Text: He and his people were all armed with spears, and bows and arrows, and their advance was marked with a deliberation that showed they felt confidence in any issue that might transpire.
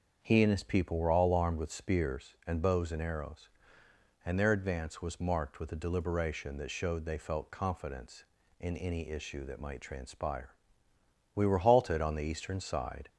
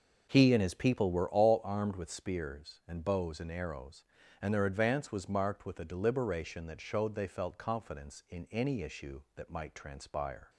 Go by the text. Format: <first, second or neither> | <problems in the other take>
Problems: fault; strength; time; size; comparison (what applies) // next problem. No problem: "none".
second | starts louder than the rest; until 1.2 s; 6.5 dB // goes on to say "We were halted on the eastern side"; strong; from 11.3 s on; 1.7 s long